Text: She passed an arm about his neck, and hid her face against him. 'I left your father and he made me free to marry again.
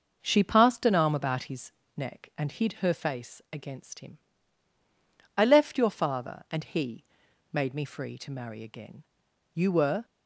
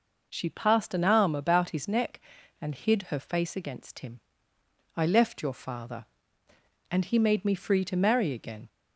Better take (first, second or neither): second